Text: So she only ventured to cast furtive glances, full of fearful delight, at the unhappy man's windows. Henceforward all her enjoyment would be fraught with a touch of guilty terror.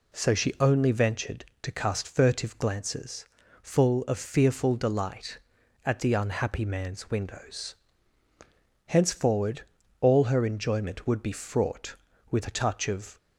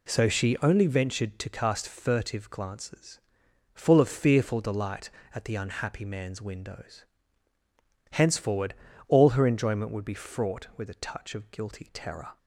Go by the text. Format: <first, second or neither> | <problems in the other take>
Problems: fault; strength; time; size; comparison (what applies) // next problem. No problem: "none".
second | pauses between "Henceforward" and "all"; at 9.6 s; 0.38 s long; slight in the second // stops before "guilty terror"; at 13.1 s